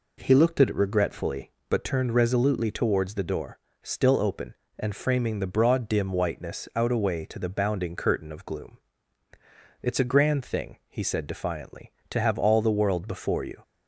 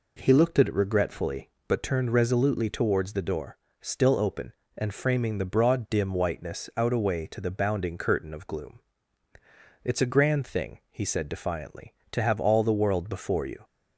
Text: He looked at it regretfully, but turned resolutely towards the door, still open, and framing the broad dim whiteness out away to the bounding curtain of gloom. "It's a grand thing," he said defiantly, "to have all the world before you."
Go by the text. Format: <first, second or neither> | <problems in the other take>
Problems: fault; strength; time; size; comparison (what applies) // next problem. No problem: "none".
neither | none